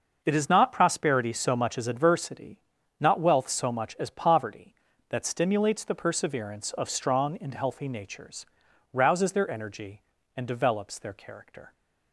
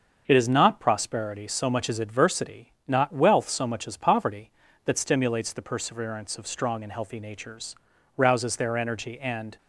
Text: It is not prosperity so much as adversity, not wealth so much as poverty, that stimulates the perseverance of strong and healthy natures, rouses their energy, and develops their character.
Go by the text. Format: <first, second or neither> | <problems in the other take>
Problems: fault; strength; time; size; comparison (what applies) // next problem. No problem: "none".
first | starts louder than the rest; until 1.2 s; 6.5 dB; noticeable in the first // stops before "develops their character"; at 9.5 s